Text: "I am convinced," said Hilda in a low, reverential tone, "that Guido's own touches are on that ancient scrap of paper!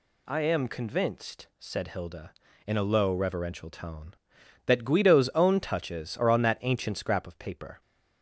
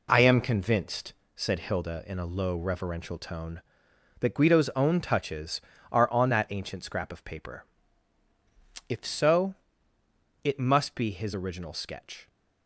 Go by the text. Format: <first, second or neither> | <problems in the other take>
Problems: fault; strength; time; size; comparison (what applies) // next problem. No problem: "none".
first | goes on to say "If so it must be his original sketch"; strong; from 8.8 s on; 3.4 s long